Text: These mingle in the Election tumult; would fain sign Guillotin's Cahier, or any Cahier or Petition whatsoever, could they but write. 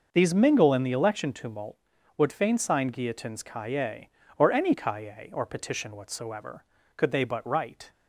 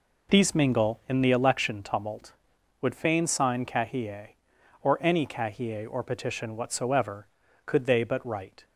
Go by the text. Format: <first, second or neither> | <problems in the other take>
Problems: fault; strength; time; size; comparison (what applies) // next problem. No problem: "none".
first | skips "Guillotin's"; at 3.6 s